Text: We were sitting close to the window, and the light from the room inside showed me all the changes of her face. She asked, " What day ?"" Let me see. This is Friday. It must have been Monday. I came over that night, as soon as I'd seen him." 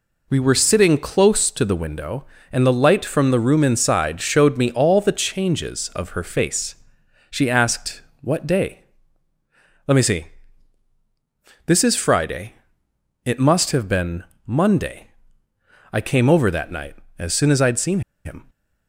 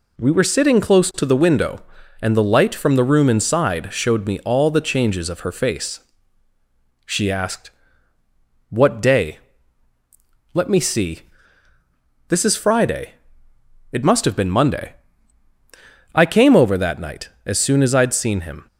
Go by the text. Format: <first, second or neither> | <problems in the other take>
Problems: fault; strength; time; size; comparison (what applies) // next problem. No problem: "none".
second | pauses between "been" and "Monday"; slight; at 14.2 s; 0.22 s long // pauses between "seen" and "him"; slight; at 17.9 s; 0.25 s long